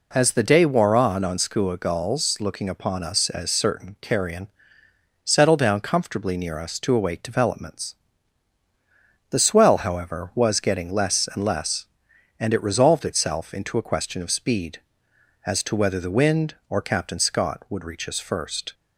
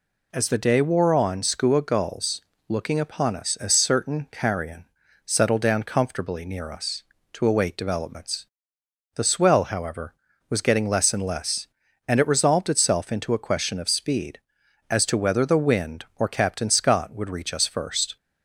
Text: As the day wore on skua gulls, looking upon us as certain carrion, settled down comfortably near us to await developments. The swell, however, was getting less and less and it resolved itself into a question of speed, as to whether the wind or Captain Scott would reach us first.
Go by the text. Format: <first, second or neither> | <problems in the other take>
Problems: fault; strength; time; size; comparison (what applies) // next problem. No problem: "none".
second | says "on" twice; at 1.2 s